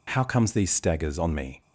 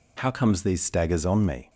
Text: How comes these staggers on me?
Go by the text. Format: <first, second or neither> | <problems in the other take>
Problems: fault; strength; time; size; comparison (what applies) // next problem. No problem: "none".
neither | none